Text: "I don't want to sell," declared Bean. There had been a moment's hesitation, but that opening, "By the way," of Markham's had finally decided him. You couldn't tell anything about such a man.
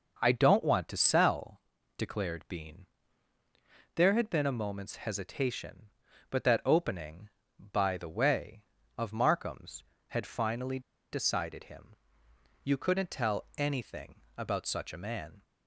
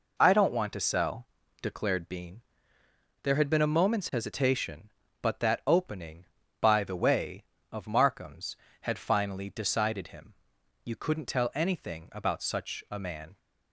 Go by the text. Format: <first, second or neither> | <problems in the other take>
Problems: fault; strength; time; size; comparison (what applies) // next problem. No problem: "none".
second | pauses between "finally" and "decided"; slight; at 10.7 s; 0.32 s long // pauses between "anything" and "about"; slight; at 14.2 s; 0.16 s long